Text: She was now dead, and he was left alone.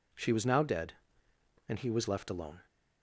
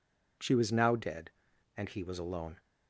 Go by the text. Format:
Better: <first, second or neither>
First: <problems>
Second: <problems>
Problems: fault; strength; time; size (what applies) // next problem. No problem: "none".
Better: first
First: none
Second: skips "left"; at 2.1 s